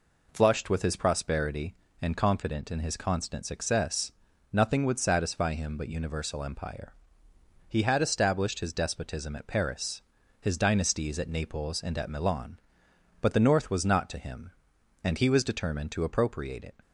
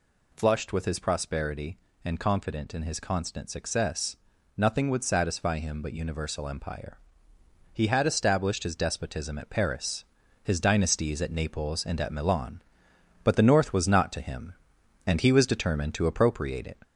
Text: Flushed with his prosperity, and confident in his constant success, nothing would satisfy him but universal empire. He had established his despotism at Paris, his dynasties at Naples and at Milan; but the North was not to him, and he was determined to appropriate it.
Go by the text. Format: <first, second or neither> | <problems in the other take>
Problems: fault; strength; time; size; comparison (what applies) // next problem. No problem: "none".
first | gets louder; slight; throughout; 2 dB